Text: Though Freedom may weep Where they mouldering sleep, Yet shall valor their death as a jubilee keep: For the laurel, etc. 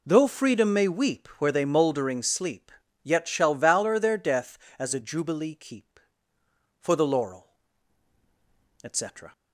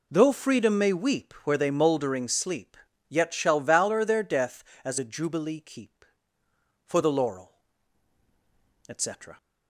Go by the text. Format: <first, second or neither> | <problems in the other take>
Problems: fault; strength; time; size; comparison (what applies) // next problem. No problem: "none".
neither | none